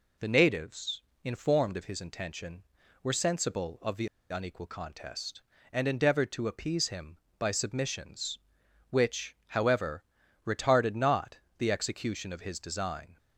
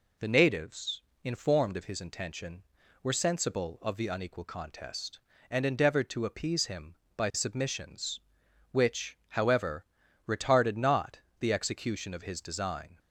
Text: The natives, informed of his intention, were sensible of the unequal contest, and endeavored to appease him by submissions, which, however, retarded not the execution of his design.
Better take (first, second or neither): second